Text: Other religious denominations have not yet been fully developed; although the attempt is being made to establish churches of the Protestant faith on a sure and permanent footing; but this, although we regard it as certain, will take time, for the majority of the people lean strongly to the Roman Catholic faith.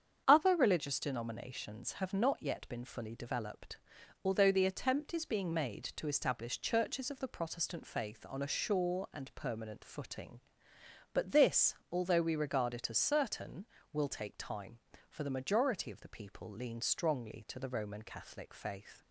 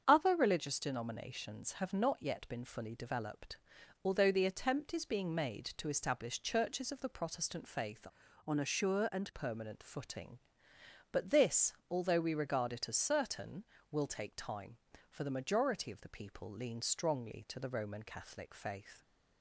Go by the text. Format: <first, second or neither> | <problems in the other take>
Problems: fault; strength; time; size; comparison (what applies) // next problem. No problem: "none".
first | starts louder than the rest; strong; until 1.0 s; 7 dB; strong in the first // changes voice from "on" to "and"; from 8.4 to 9.3 s; 0.9 s long